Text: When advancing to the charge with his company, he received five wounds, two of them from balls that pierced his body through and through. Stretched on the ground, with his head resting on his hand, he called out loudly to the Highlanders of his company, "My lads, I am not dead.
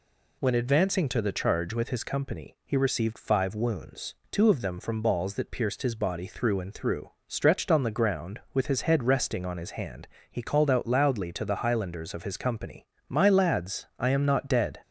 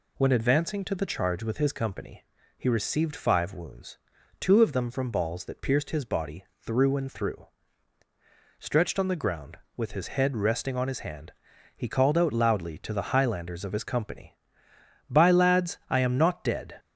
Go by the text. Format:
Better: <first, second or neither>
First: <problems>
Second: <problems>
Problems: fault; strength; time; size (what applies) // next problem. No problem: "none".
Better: first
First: none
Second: pauses between "body" and "through"; slight; at 6.4 s; 0.16 s long // says "By" for "My"; at 15.0 s